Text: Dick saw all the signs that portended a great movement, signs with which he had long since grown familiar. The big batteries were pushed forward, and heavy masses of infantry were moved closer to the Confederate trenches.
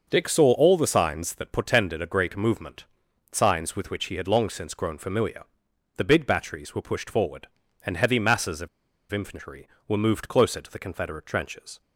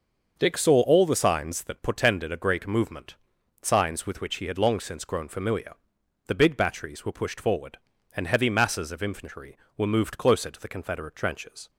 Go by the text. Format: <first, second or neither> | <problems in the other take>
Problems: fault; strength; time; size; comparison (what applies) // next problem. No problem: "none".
second | starts louder than the rest; until 1.1 s; 6 dB; also in the second // pauses between "of" and "infantry"; at 8.6 s; 0.44 s long